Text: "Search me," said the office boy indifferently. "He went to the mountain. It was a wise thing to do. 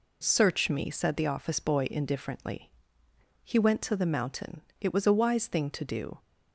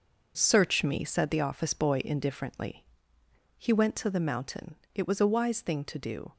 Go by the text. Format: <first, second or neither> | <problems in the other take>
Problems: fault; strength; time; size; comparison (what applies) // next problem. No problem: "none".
first | gets quieter; strong; throughout; 8 dB